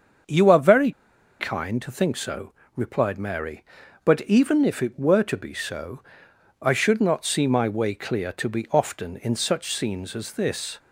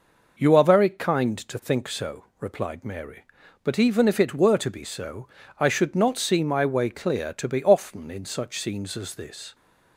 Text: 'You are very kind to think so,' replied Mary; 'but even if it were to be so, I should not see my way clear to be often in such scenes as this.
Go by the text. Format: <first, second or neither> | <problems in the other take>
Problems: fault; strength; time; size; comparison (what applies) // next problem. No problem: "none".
second | starts louder than the rest; until 1.7 s; 7 dB // pauses between "very" and "kind"; noticeable; at 0.9 s; 0.48 s long